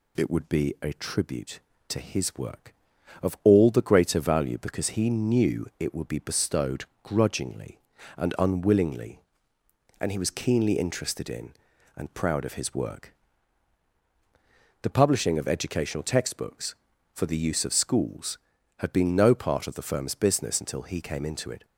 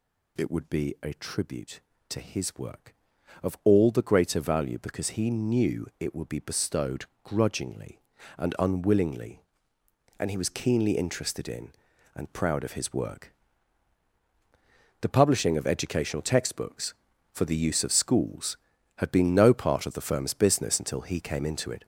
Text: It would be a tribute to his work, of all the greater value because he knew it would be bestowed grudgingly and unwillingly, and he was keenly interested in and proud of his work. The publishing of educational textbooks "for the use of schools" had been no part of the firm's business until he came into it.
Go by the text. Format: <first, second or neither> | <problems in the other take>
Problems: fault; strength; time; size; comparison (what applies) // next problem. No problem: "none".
first | gets louder; noticeable; throughout; 5.5 dB // pauses between "bestowed" and "grudgingly"; slight; at 7.0 s; 0.18 s long; slight in the first